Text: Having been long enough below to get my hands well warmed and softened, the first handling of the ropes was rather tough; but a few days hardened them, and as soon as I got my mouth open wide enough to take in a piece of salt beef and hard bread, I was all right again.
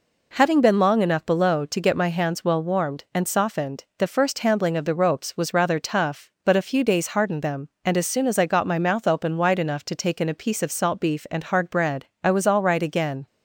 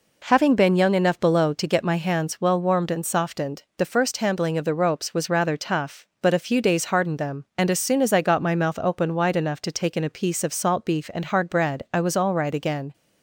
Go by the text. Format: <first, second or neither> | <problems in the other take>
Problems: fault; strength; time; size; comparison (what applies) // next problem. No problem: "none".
first | says "young" for "long"; at 0.7 s